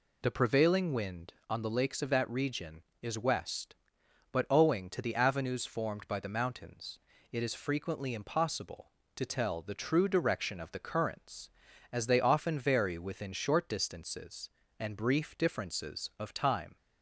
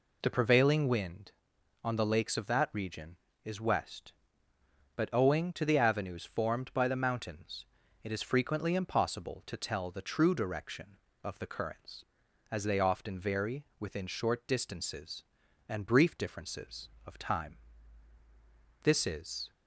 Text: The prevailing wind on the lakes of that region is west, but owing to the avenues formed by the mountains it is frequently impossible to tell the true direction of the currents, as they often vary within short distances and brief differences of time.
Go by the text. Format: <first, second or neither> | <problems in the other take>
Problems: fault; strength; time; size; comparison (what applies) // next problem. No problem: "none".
first | pauses between "mountains" and "it"; at 7.6 s; 0.38 s long; slight in the first // goes on to say "This is"; noticeable; from 18.8 s on; 0.68 s long